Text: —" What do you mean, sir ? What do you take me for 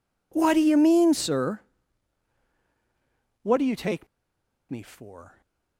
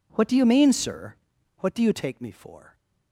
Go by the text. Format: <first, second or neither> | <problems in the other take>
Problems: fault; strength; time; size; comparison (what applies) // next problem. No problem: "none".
second | pauses between "take" and "me"; noticeable; at 4.0 s; 0.63 s long